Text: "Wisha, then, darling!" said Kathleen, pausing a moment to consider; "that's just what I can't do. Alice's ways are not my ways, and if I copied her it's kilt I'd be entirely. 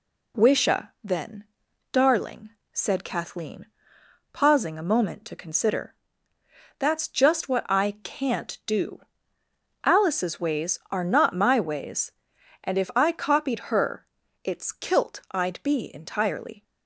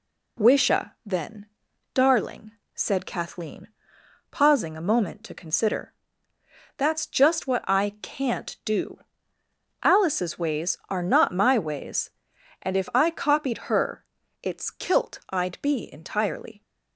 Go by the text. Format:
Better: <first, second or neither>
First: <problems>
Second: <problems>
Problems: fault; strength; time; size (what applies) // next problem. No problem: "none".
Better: neither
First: pauses between "her" and "it's"; at 14.0 s; 0.40 s long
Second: pauses between "her" and "it's"; at 14.0 s; 0.40 s long